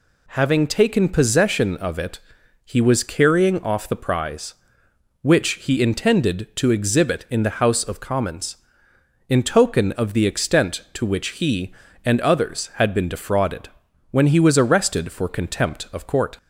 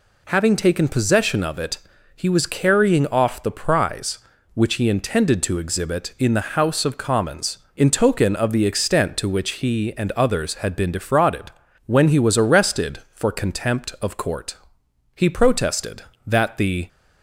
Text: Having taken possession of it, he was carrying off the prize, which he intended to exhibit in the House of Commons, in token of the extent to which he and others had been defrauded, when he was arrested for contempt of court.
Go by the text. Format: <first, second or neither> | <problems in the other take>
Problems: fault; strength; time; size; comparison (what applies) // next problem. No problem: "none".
first | goes on to say "He protested that the"; strong; from 15.1 s on; 1.7 s long